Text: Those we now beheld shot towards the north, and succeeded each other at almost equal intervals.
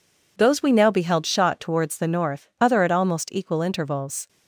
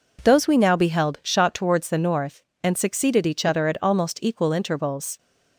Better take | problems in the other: second | skips "and succeeded each"; at 2.5 s

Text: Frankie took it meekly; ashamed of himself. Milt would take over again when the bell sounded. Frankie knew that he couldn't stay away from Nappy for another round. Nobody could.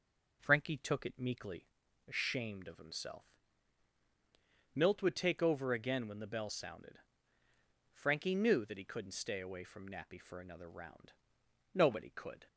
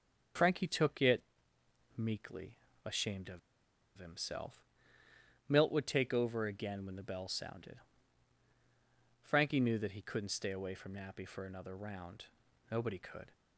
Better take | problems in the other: first | starts louder than the rest; until 2.1 s; 7 dB // pauses between "it" and "meekly"; noticeable; at 1.2 s; 0.74 s long // pauses between "of" and "himself"; noticeable; at 3.3 s; 0.58 s long

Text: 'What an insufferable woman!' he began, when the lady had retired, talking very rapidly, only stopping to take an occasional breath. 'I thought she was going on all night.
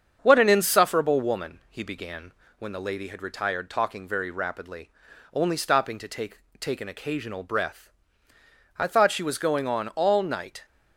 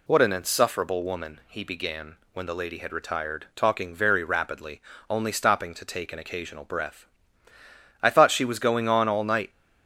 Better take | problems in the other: second | starts louder than the rest; strong; until 1.2 s; 7.5 dB // says "take" twice; at 6.5 s

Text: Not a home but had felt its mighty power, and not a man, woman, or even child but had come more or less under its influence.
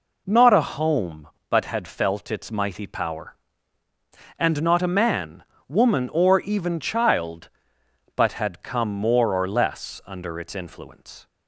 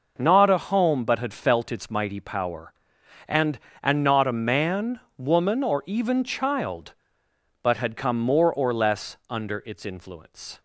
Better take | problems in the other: first | says "and" twice; at 3.8 s

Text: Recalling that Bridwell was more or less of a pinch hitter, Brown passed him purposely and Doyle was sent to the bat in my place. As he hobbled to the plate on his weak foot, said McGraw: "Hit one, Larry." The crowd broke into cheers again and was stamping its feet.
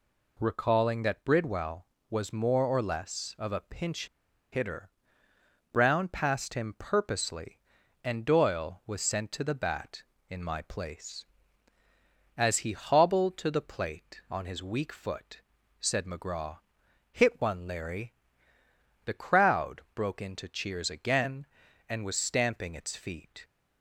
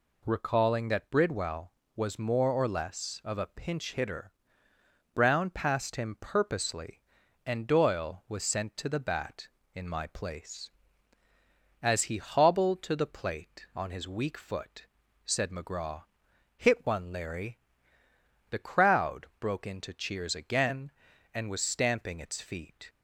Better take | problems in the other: second | pauses between "pinch" and "hitter"; at 4.0 s; 0.44 s long

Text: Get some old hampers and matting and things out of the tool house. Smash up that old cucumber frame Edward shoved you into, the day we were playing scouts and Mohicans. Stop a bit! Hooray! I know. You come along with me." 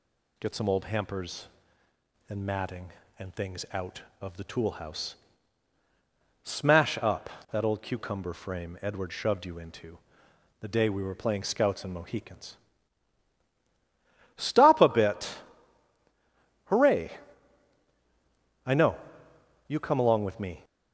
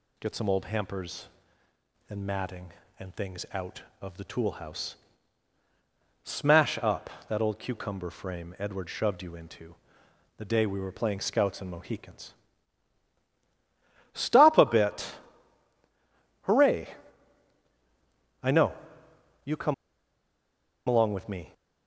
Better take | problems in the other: first | pauses between "come" and "along"; at 19.7 s; 1.1 s long

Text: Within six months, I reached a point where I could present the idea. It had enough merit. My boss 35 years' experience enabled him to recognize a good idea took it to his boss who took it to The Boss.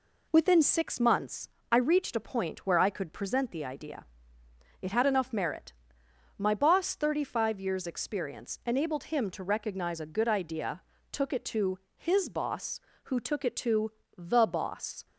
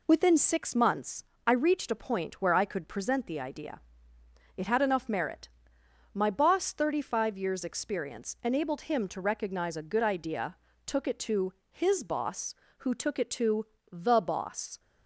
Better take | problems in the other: neither | pauses between "idea" and "took"; slight; the same in both // pauses between "to" and "his"; slight; the same in both // pauses between "to" and "The"; slight; the same in both

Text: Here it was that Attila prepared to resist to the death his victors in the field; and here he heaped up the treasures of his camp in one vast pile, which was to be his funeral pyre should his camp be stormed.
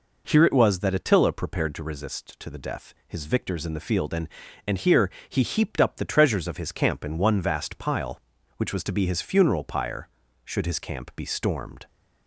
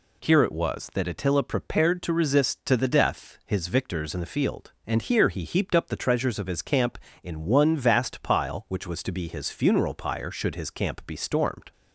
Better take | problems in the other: second | says "and" twice; at 4.6 s // pauses between "here" and "he"; slight; at 5.0 s; 0.22 s long

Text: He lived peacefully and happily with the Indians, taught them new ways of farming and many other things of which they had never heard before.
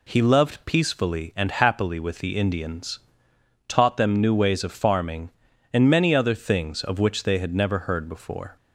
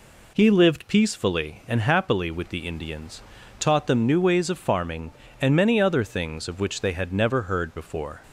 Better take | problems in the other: second | says "loved" for "lived"; at 0.2 s

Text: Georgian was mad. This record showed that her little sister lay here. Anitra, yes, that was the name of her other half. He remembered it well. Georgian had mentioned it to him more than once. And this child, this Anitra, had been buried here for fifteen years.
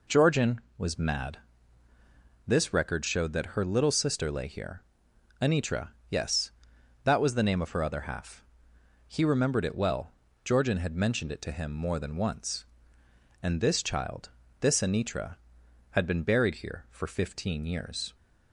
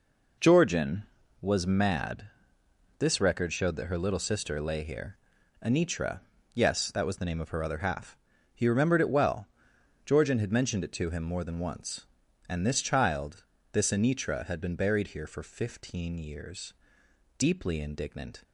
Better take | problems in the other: first | goes on to say "Deeply indignant"; noticeable; from 17.3 s on; 1.0 s long

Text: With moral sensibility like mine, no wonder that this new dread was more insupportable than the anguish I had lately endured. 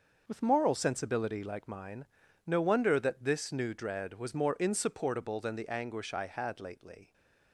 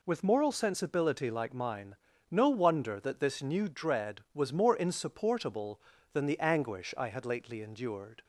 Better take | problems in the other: second | starts louder than the rest; until 1.2 s; 6 dB // stops before "endured"; at 7.1 s

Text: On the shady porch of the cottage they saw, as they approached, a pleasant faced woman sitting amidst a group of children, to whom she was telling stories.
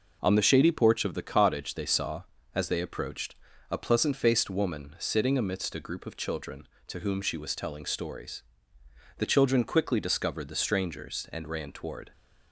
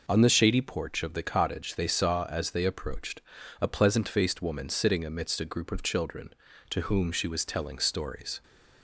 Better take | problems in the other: second | goes on to say "The children quickly discovered the strangers and ran toward"; strong; from 9.1 s on; 2.9 s long

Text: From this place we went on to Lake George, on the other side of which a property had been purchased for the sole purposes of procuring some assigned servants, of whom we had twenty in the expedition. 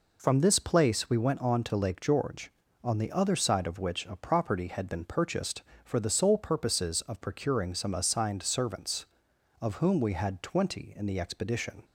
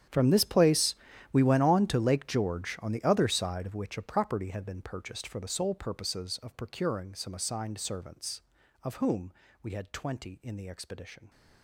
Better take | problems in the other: first | gets quieter; strong; throughout; 19 dB // pauses between "place" and "we"; at 0.9 s; 0.38 s long // pauses between "whom" and "we"; slight; at 9.3 s; 0.30 s long

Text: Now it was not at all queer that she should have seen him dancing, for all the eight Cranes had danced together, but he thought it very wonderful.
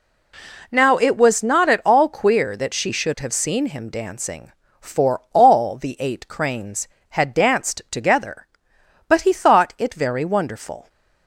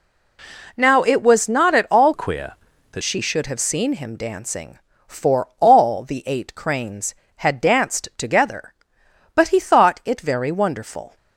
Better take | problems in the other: first | changes voice from "queer" to "that"; from 2.1 to 3.0 s; 0.9 s long

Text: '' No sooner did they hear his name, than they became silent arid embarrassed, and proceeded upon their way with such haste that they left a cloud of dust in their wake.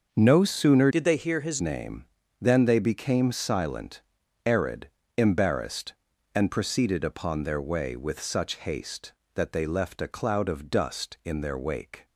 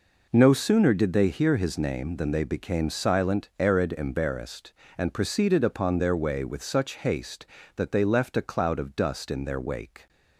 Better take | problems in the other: second | starts louder than the rest; until 1.1 s; 6 dB // changes voice from "did" to "his"; from 0.9 to 1.6 s; 0.7 s long // pauses between "silent" and "arid"; noticeable; at 3.9 s; 0.46 s long // pauses between "arid" and "embarrassed"; slight; at 4.8 s; 0.30 s long

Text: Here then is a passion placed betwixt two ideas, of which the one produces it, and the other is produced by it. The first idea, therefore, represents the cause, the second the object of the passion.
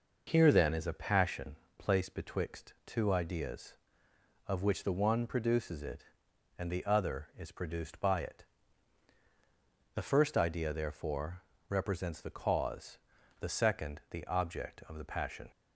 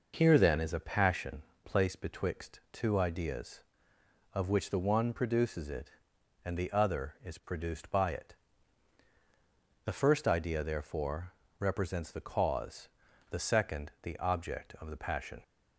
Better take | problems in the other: neither | pauses between "passion" and "placed"; slight; the same in both

